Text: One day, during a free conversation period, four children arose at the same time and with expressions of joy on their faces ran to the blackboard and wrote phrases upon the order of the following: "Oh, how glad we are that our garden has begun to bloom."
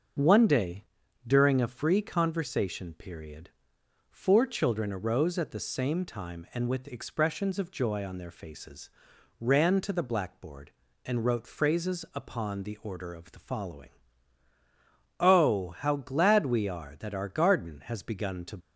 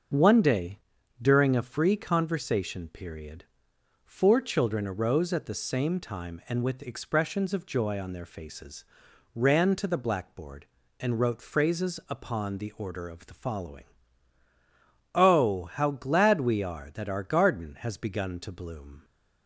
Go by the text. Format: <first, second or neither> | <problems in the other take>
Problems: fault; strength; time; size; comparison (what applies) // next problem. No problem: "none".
second | starts louder than the rest; until 1.6 s; 6 dB; also in the second // pauses between "faces" and "ran"; noticeable; at 8.8 s; 0.50 s long; noticeable in the second // stops before "bloom"; at 18.6 s